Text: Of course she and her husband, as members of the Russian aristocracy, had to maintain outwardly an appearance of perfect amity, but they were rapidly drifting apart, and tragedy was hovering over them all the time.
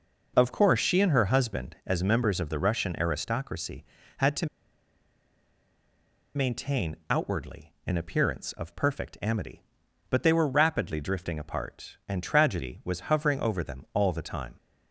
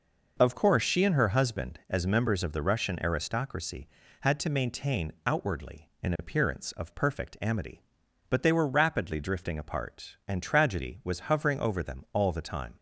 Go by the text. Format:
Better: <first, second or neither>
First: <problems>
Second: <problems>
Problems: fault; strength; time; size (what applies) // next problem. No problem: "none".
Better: second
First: pauses between "to" and "maintain"; strong; at 4.4 s; 1.8 s long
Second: none